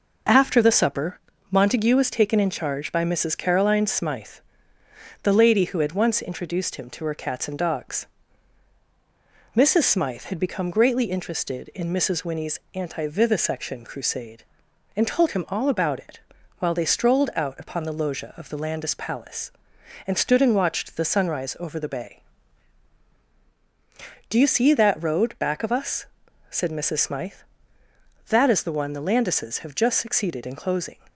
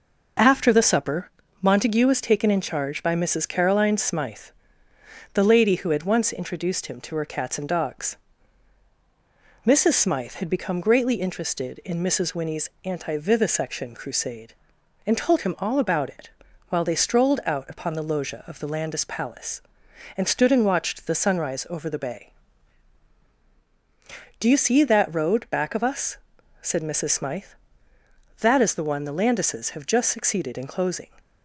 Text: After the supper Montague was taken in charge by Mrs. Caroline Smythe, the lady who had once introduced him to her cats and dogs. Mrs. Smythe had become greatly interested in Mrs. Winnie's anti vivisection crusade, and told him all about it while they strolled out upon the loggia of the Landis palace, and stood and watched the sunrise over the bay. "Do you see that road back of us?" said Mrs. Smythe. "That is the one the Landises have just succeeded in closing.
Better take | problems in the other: neither | pauses between "supper" and "Montague"; slight; the same in both // pauses between "it" and "while"; the same in both

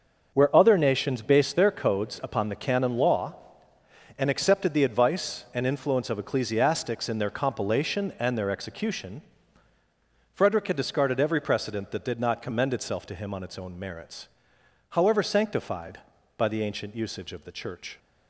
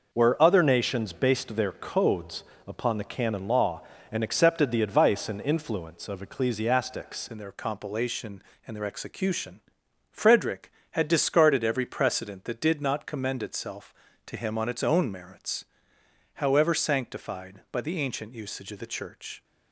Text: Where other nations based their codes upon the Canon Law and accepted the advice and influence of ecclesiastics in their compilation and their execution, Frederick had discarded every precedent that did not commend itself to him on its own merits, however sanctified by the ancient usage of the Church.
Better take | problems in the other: first | pauses between "codes" and "upon"; slight; at 2.4 s; 0.24 s long // changes voice at "in"; from 7.3 s on; 12.1 s long

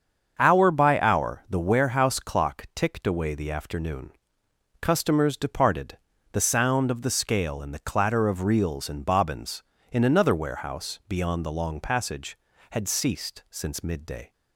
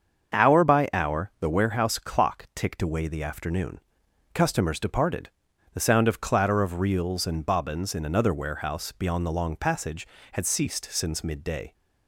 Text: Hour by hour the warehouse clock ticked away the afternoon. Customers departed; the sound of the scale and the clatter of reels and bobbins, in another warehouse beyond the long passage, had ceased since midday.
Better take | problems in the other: first | starts louder than the rest; until 1.5 s; 7 dB; also in the first // skips "the scale and the"; at 6.2 s

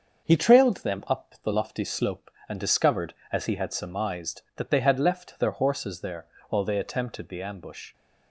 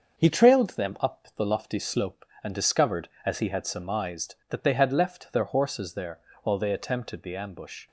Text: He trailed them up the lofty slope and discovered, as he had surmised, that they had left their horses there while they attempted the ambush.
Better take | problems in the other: neither | starts louder than the rest; the same in both // pauses between "there" and "while"; slight; the same in both

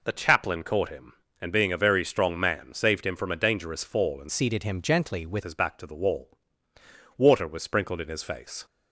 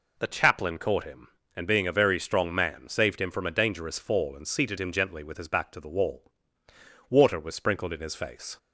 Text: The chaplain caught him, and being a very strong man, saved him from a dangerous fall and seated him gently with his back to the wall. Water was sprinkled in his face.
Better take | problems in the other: second | changes voice from "seated" to "with"; from 4.2 to 5.4 s; 1.2 s long

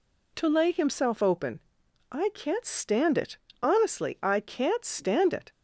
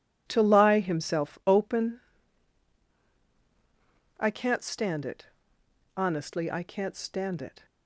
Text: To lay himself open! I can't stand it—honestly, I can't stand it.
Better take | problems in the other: first | says "lie" for "lay"; at 0.4 s

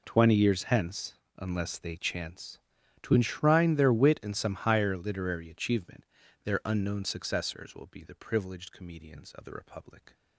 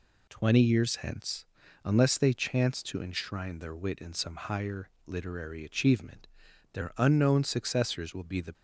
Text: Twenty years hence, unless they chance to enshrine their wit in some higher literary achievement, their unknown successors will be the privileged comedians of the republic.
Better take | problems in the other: first | pauses between "higher" and "literary"; slight; at 4.8 s; 0.16 s long // stops before "privileged comedians of the republic"; at 8.5 s

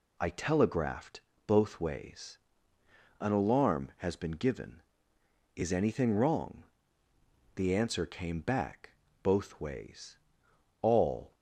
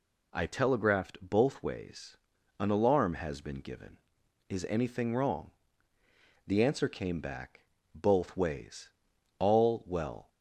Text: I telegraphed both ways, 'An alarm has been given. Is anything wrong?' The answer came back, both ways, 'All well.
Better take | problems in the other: second | pauses between "telegraphed" and "both"; slight; at 1.2 s; 0.26 s long // stops before "well"; at 11.3 s

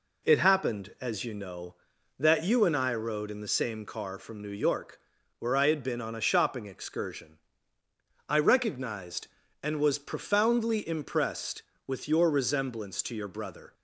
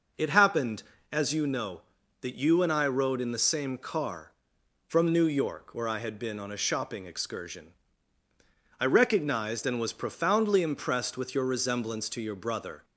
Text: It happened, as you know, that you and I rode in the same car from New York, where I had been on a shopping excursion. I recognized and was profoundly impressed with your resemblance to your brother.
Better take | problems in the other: neither | none

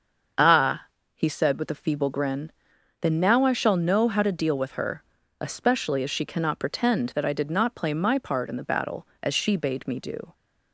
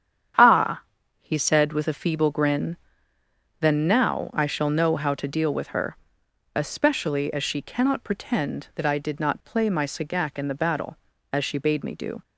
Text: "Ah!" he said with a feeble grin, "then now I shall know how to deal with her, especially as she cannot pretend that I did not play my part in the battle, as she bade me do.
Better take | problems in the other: first | starts louder than the rest; strong; until 1.7 s; 9 dB; also in the first // says "sagac" for "part"; at 9.8 s

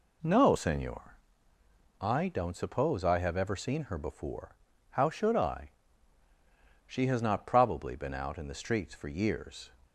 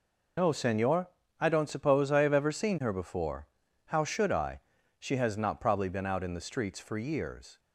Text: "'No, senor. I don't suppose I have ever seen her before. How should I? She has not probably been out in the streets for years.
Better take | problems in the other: first | loses the start of "No"; at 0.3 s; 80 ms

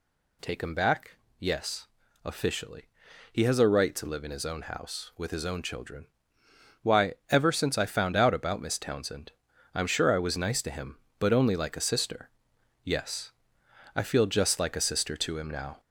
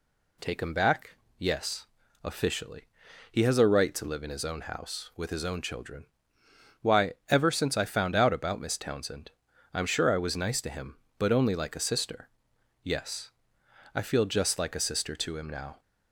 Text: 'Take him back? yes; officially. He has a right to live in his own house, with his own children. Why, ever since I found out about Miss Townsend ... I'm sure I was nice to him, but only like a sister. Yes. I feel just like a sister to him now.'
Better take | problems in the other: second | gets louder; noticeable; throughout; 4 dB

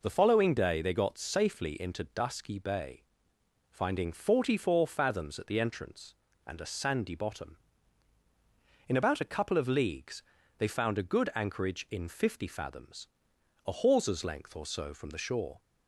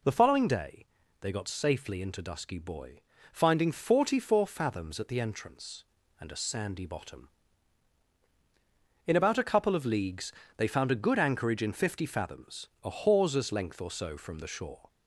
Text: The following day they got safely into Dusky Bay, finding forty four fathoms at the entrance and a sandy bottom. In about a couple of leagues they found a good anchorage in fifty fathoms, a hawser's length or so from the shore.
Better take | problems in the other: first | pauses between "day" and "they"; slight; at 0.8 s; 0.34 s long // says "Boy" for "Bay"; at 2.5 s // pauses between "leagues" and "they"; slight; at 10.3 s; 0.26 s long; slight in the first

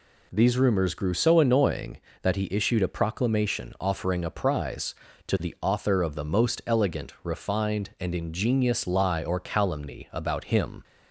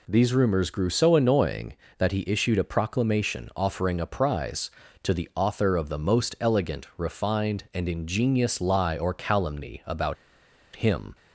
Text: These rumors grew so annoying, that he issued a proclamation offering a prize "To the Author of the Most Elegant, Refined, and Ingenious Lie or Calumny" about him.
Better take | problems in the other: first | pauses between "about" and "him"; noticeable; at 10.1 s; 0.59 s long

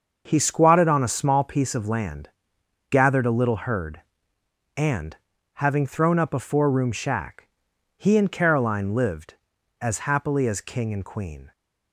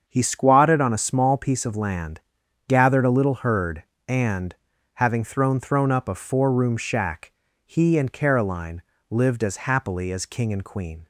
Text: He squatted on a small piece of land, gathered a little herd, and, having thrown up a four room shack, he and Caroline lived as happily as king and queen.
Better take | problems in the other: first | starts louder than the rest; until 1.0 s; 7 dB; also in the first // says "thrown" twice; at 5.5 s // pauses between "Caroline" and "lived"; slight; at 8.8 s; 0.28 s long

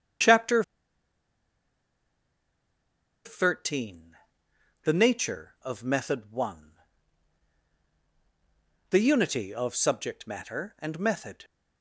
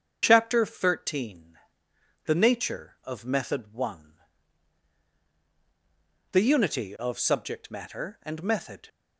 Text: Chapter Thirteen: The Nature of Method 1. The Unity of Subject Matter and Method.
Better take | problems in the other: second | starts louder than the rest; strong; until 3.8 s; 7.5 dB; strong in the second // pauses between "Chapter" and "Thirteen"; strong; at 0.6 s; 2.6 s long

